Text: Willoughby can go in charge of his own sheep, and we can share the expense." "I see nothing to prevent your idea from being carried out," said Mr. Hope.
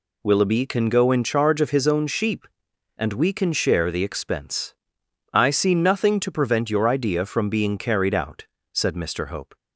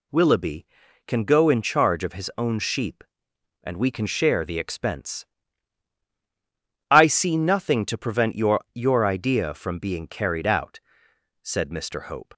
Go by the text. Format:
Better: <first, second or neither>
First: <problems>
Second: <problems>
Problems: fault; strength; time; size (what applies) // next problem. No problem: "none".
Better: first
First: none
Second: says "your" twice; at 8.7 s